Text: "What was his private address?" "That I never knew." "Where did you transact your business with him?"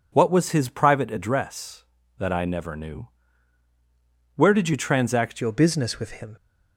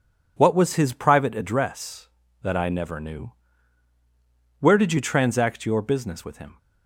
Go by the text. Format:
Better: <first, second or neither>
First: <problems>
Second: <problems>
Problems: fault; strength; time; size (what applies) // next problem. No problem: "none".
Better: second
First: changes voice at "your"; from 5.4 s on; 0.9 s long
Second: none